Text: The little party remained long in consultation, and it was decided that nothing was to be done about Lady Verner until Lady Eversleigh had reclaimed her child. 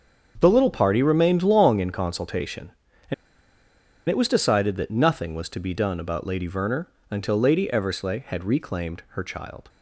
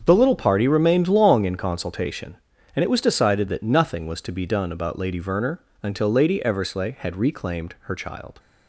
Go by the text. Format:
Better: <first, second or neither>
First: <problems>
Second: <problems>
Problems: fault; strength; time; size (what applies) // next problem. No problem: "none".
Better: second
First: starts louder than the rest; strong; until 1.4 s; 7 dB // pauses between "and" and "it"; noticeable; at 3.1 s; 0.94 s long // pauses between "Verner" and "until"; slight; at 6.8 s; 0.22 s long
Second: starts louder than the rest; strong; until 1.0 s; 7 dB // pauses between "Verner" and "until"; slight; at 5.6 s; 0.22 s long